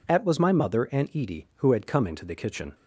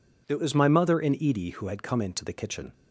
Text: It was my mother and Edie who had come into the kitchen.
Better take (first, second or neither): second